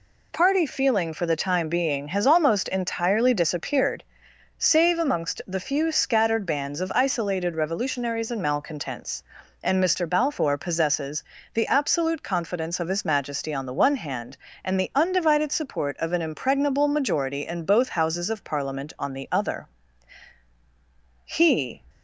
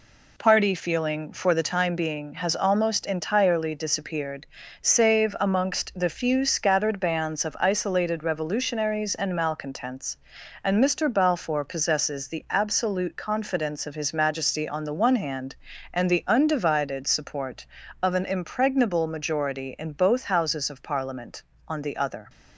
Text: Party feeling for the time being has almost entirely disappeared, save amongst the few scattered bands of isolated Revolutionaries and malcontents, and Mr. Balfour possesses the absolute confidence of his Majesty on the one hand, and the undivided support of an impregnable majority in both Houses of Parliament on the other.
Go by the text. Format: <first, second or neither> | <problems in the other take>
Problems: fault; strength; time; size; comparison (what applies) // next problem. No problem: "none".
second | pauses between "possesses" and "the"; slight; at 11.2 s; 0.32 s long // goes on to say "He"; from 21.2 s on; 0.58 s long